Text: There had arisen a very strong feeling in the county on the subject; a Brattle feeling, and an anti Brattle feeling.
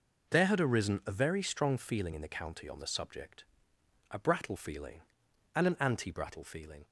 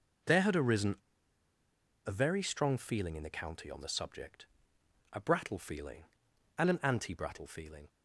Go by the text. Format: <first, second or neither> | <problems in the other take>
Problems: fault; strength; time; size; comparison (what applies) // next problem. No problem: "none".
first | pauses between "arisen" and "a"; at 0.9 s; 1.0 s long